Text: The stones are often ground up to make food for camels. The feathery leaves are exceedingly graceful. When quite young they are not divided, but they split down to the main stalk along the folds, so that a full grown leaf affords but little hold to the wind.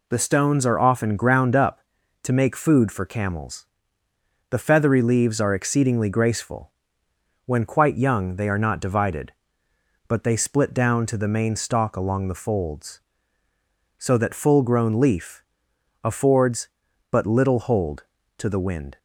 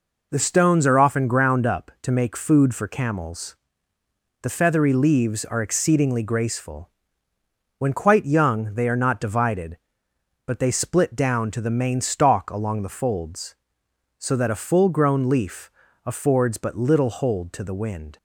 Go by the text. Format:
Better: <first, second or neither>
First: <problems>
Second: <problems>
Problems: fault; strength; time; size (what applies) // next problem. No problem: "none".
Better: second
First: skips "a"; at 14.3 s // pauses between "leaf" and "affords"; noticeable; at 15.4 s; 0.60 s long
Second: pauses between "leaf" and "affords"; at 15.6 s; 0.38 s long